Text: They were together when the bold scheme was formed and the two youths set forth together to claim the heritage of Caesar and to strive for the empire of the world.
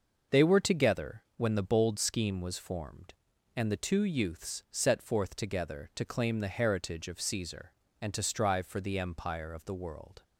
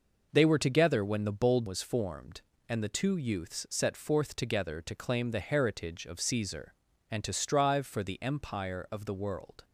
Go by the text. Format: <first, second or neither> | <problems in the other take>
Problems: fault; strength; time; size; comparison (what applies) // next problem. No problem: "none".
first | skips "scheme"; at 1.6 s